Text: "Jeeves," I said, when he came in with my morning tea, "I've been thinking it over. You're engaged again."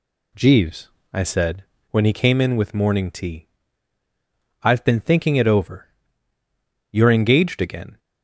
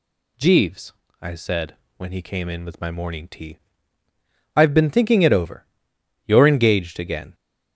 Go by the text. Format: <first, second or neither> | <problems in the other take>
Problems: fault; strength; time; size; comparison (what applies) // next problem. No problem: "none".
second | skips "my"; at 2.7 s